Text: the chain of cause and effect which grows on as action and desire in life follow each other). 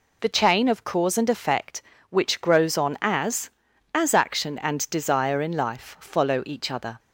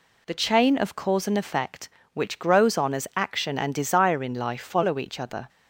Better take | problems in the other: second | says "as" twice; at 3.9 s

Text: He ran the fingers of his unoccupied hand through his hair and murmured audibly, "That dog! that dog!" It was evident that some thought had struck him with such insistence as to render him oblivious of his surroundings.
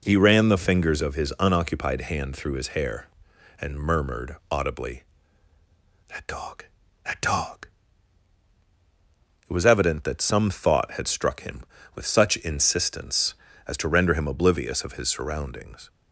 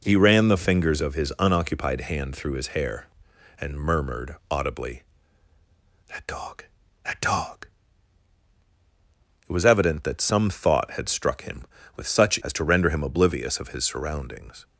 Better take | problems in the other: first | pauses between "murmured" and "audibly"; slight; at 4.3 s; 0.16 s long; slight in the first // skips "insistence"; at 12.4 s

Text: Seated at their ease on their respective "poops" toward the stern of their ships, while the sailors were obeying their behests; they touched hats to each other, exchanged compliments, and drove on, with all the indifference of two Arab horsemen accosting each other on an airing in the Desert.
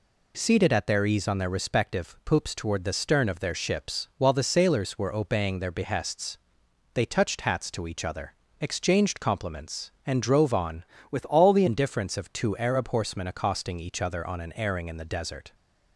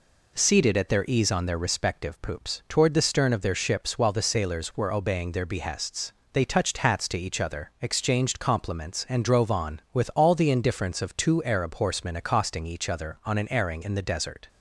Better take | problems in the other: second | changes voice from "with" to "the"; from 11.0 to 11.6 s; 0.6 s long

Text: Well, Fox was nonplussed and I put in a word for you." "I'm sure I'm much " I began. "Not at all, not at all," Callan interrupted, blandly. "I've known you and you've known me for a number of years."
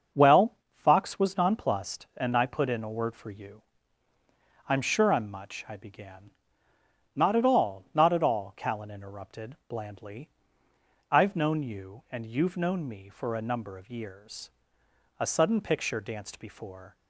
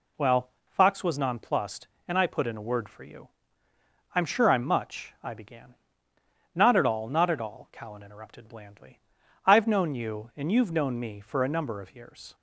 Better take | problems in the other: second | starts louder than the rest; until 1.3 s; 6.5 dB // goes on to say "A sudden picture danced before"; strong; from 15.1 s on; 1.7 s long

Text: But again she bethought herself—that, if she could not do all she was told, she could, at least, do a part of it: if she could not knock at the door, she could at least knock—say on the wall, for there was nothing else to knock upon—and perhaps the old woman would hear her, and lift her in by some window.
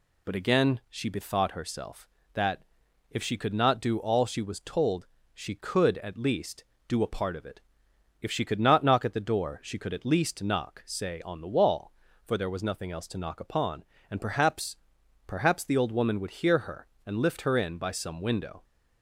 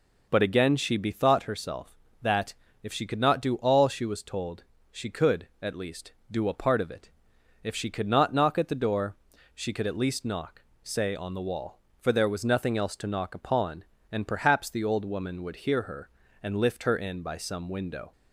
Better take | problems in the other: second | says "perhaps" twice; at 15.2 s

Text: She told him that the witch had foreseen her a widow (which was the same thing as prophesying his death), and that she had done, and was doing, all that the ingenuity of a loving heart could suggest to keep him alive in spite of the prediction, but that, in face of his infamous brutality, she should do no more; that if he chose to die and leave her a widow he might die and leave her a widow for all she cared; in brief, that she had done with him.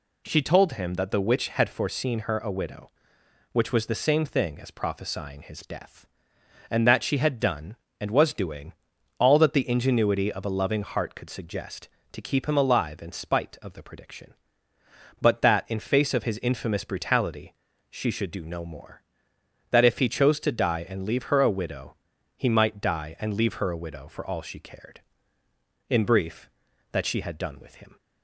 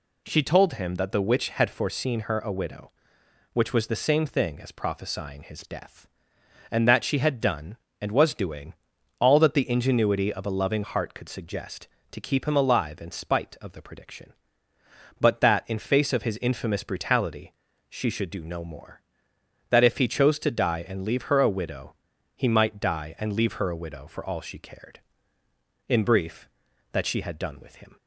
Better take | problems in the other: neither | pauses between "widow" and "he"; the same in both

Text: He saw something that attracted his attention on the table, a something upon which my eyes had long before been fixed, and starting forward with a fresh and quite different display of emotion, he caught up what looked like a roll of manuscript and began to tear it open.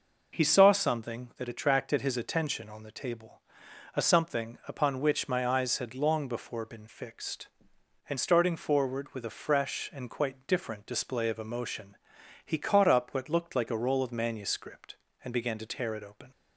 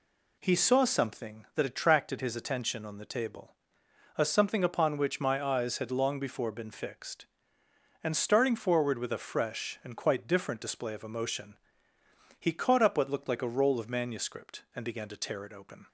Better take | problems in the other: neither | none

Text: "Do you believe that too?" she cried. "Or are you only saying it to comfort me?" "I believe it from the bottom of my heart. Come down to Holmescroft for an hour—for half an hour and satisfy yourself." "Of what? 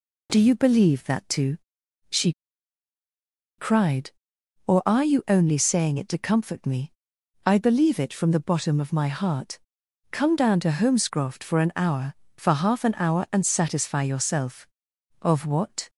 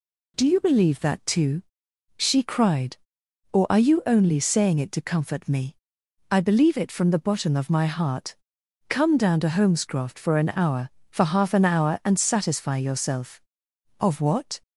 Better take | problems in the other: second | pauses between "she" and "cried"; strong; at 2.3 s; 1.2 s long

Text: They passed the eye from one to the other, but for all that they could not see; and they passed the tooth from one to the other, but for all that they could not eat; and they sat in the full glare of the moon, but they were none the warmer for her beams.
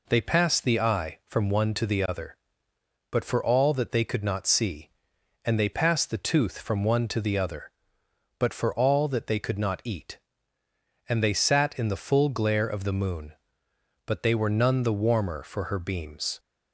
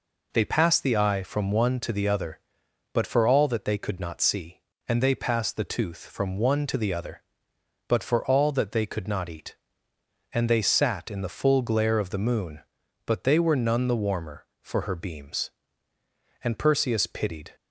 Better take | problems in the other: first | goes on to say "And Perseus pitied"; noticeable; from 16.4 s on; 1.1 s long

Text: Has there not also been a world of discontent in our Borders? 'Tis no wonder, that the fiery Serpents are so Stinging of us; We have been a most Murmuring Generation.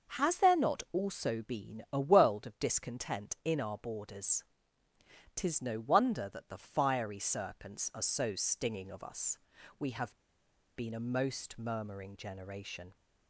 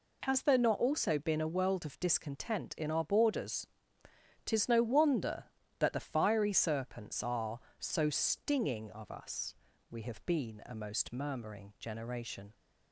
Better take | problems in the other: second | starts louder than the rest; until 1.2 s; 6 dB // pauses between "have" and "been"; noticeable; at 10.1 s; 0.59 s long

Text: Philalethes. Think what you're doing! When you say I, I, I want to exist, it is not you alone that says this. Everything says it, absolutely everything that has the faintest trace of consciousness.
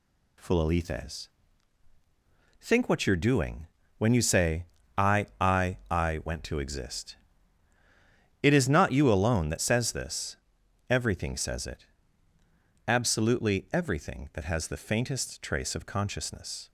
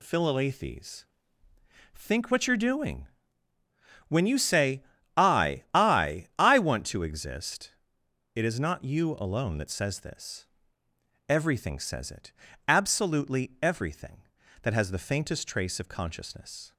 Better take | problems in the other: second | pauses between "say" and "I"; slight; at 4.6 s; 0.32 s long; slight in the second // says "went" for "want"; at 6.2 s

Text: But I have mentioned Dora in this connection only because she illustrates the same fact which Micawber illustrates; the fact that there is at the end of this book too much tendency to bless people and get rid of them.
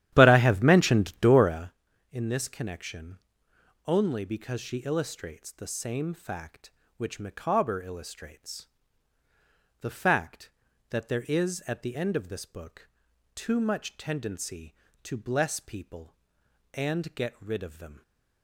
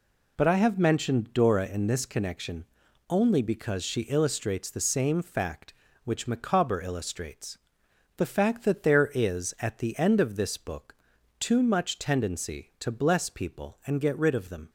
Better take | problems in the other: second | starts louder than the rest; strong; until 1.7 s; 12 dB // pauses between "connection" and "only"; noticeable; at 3.1 s; 0.68 s long; also in the second // pauses between "book" and "too"; noticeable; at 12.8 s; 0.46 s long; also in the second

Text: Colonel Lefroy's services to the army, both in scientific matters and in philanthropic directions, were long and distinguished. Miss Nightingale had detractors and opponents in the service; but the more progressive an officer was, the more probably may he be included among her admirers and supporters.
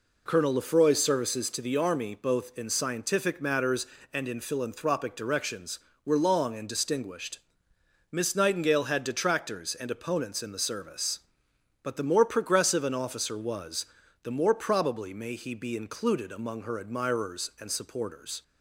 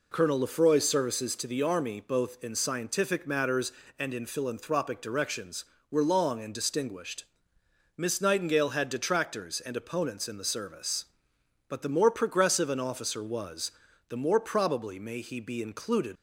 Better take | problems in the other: first | stops before "among her admirers and supporters"; at 16.1 s

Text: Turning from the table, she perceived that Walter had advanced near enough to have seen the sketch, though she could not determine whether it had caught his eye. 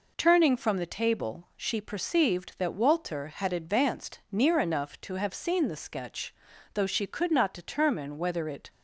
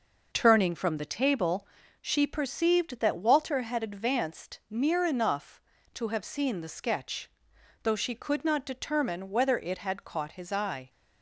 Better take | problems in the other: second | stops before "had caught his eye"; at 8.6 s

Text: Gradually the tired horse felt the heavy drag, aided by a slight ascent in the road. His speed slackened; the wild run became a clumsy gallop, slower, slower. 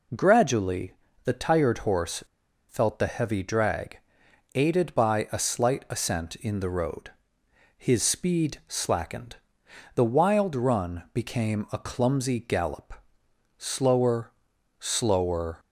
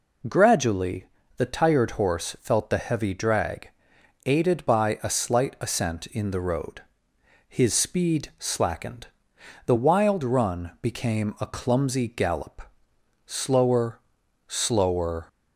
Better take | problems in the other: second | pauses between "Gradually" and "the"; slight; at 0.9 s; 0.30 s long; slight in the second // pauses between "horse" and "felt"; at 2.2 s; 0.45 s long

